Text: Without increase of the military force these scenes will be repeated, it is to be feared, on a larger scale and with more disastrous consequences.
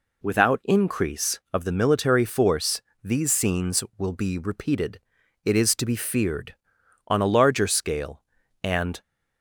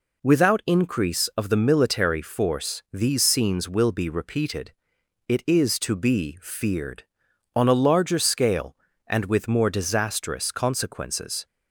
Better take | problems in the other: second | pauses between "force" and "these"; slight; at 2.8 s; 0.22 s long // stops before "with more disastrous consequences"; at 9.0 s

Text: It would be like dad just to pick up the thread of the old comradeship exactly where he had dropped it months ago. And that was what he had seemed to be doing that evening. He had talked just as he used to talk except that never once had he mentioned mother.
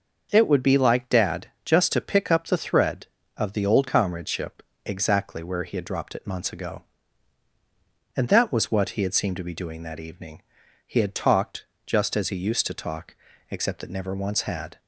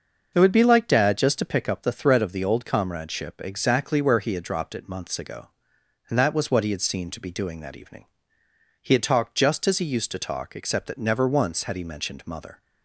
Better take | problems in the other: second | starts louder than the rest; until 1.3 s; 6 dB; noticeable in the second // pauses between "dad" and "just"; slight; at 1.4 s; 0.18 s long // pauses between "comradeship" and "exactly"; slight; at 4.6 s; 0.24 s long // pauses between "talked" and "just"; slight; at 11.6 s; 0.20 s long // pauses between "talk" and "except"; slight; at 13.1 s; 0.34 s long // stops before "he mentioned mother"; at 14.7 s

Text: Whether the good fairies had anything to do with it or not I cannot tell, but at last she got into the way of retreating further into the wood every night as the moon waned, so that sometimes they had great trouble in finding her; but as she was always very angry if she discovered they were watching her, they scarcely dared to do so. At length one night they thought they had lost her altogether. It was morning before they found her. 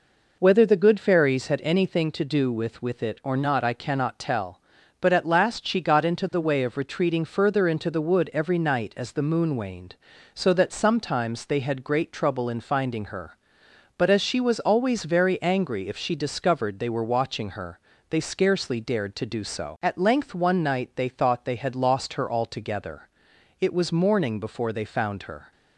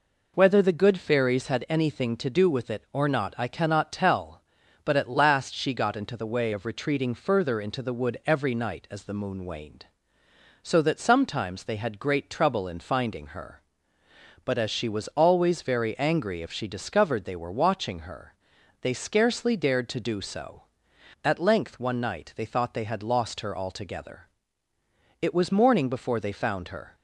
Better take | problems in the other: second | says "with" twice; at 2.8 s

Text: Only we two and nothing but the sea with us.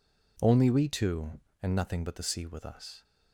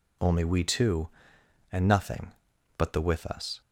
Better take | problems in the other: first | skips "sea"; at 3.0 s

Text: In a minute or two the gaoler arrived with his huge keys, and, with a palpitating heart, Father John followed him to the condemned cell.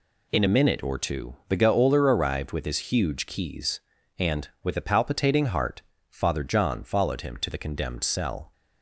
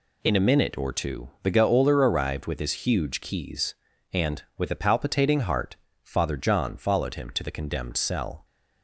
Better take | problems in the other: neither | none

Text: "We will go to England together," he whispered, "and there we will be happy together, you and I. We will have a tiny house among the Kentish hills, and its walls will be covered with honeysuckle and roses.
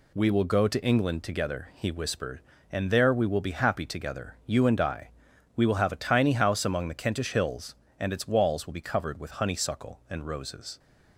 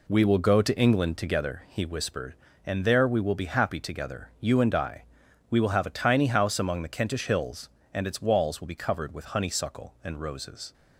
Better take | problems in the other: first | starts louder than the rest; slight; until 1.6 s; 2.5 dB

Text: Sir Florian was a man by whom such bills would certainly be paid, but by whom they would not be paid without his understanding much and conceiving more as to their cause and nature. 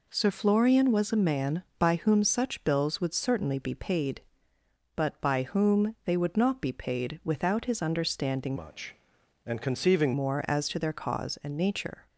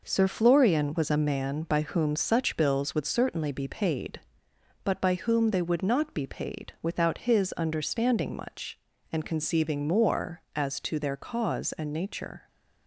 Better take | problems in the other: second | changes voice from "much" to "conceiving"; from 8.5 to 10.1 s; 1.6 s long

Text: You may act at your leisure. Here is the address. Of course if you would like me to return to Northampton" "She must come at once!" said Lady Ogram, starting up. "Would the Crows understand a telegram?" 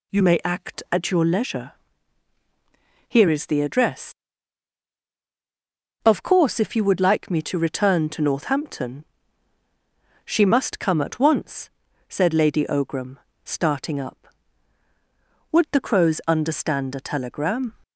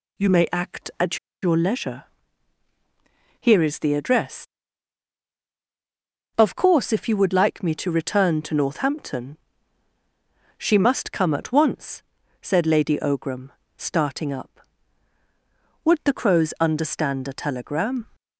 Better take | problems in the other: first | pauses between "at" and "your"; slight; at 1.1 s; 0.24 s long // pauses between "Northampton" and "She"; at 9.3 s; 1.2 s long; also in the first

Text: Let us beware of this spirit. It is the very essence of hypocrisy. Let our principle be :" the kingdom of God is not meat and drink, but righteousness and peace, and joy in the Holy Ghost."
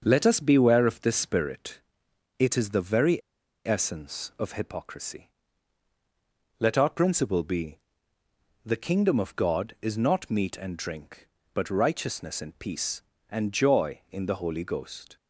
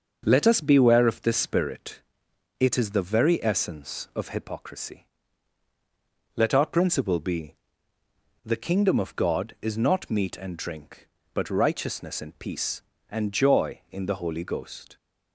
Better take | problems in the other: second | starts louder than the rest; until 1.0 s; 6.5 dB; also in the second // pauses between "very" and "essence"; noticeable; at 3.2 s; 0.46 s long

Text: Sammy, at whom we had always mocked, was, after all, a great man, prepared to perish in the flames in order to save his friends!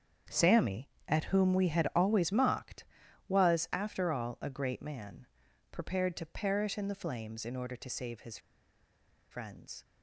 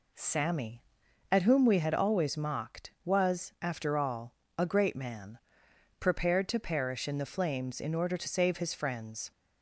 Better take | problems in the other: second | starts louder than the rest; strong; until 1.4 s; 7.5 dB // pauses between "his" and "friends"; noticeable; at 8.3 s; 0.93 s long

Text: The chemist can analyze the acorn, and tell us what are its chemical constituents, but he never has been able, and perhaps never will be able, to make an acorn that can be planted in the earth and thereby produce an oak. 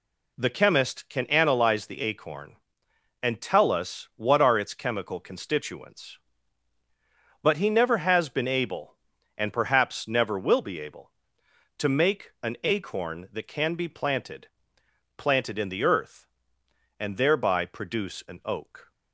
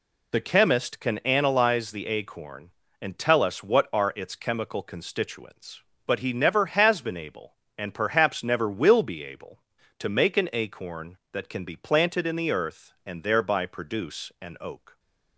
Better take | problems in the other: second | says "planted" twice; at 15.1 s

